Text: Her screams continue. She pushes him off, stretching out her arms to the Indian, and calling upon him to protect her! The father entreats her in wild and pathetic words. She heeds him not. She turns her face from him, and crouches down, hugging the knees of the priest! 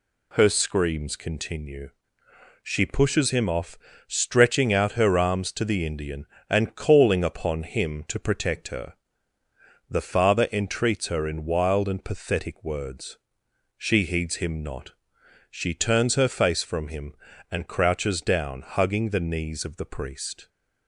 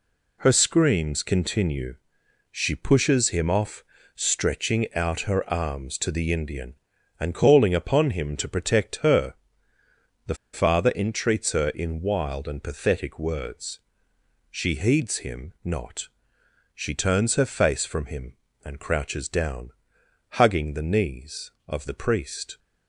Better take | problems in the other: first | pauses between "The" and "father"; slight; at 10.3 s; 0.17 s long

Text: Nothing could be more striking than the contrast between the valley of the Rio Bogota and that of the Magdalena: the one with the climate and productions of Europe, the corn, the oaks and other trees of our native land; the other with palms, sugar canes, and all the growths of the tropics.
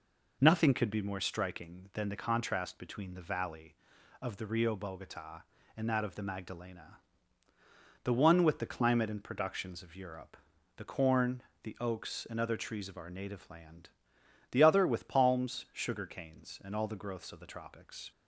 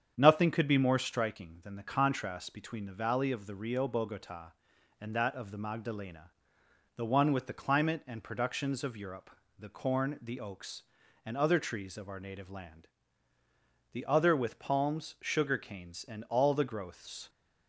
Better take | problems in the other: first | starts louder than the rest; strong; until 1.1 s; 8 dB // stops before "of the tropics"; at 17.2 s

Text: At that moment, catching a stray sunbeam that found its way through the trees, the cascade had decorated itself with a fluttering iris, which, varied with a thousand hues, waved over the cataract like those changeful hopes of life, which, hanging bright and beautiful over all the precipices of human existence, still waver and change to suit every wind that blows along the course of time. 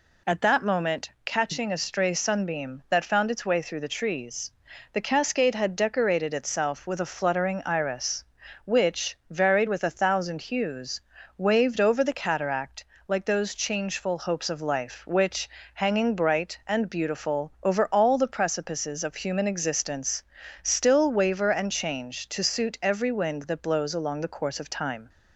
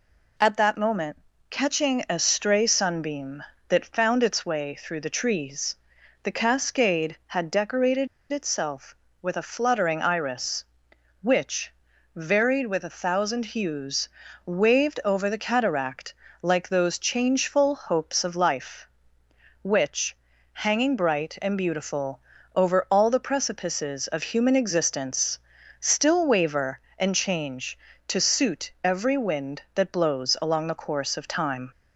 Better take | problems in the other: first | pauses between "decorated" and "itself"; slight; at 8.0 s; 0.25 s long // pauses between "cataract" and "like"; slight; at 16.1 s; 0.30 s long; slight in the first // pauses between "beautiful" and "over"; slight; at 22.1 s; 0.34 s long

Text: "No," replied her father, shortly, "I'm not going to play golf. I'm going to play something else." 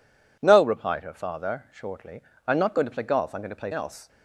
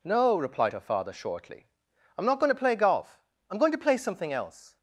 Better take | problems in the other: second | skips "something"; at 3.7 s

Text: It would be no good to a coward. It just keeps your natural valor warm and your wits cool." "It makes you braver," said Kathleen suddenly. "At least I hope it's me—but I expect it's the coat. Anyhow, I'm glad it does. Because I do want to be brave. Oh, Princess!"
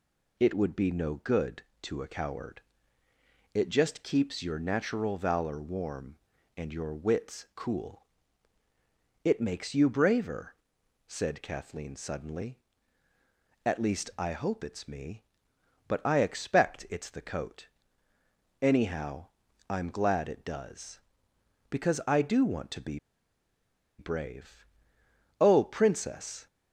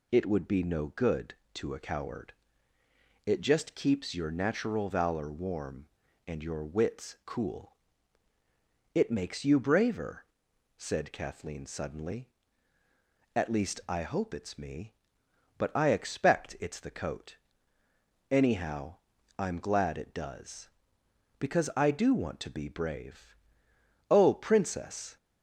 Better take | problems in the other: second | pauses between "be" and "brave"; at 22.9 s; 1.0 s long

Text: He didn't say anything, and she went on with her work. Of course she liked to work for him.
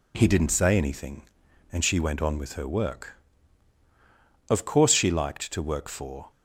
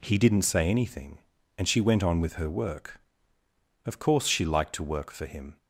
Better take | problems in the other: second | stops before "him"; at 6.2 s

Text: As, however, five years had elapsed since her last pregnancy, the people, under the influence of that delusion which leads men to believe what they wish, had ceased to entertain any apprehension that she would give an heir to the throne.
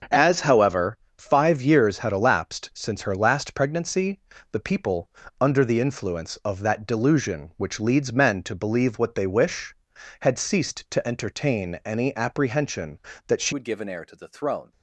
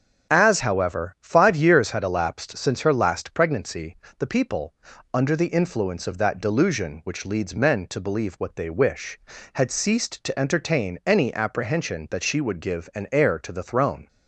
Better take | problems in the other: second | starts louder than the rest; until 1.3 s; 6.5 dB; also in the second // changes voice at "would"; from 13.5 s on; 1.2 s long

